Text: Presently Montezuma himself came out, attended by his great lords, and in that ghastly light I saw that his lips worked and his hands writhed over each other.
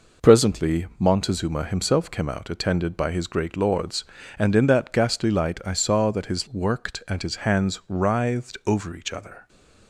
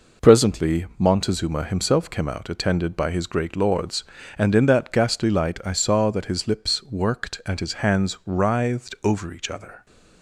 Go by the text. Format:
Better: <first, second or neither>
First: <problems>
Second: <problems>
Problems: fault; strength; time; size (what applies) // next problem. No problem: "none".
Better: second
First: skips "lips"; at 6.4 s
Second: none